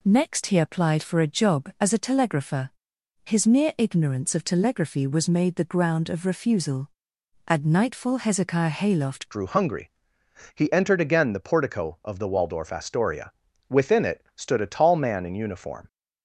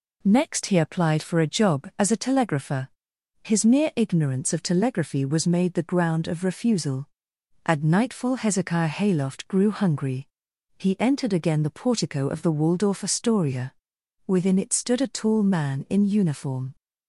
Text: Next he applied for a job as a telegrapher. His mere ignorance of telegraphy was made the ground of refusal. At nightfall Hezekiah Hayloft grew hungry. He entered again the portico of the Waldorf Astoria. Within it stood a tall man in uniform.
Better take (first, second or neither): second